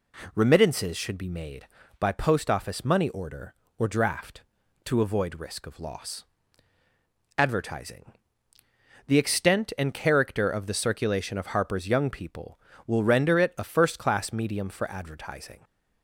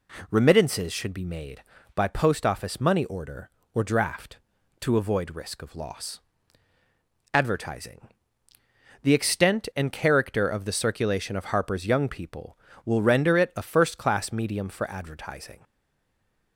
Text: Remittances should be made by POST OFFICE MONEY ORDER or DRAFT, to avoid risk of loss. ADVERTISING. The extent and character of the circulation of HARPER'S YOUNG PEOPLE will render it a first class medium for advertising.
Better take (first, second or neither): first